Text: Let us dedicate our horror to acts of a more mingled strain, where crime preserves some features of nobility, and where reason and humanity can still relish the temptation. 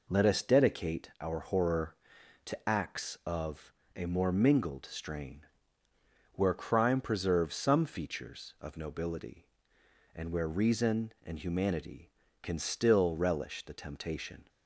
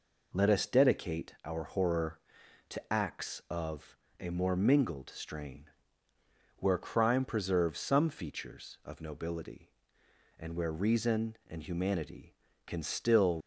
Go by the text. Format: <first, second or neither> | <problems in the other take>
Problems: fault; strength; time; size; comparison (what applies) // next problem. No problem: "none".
first | pauses between "of" and "a"; slight; at 3.9 s; 0.20 s long; slight in the first // stops before "relish the temptation"; at 13.4 s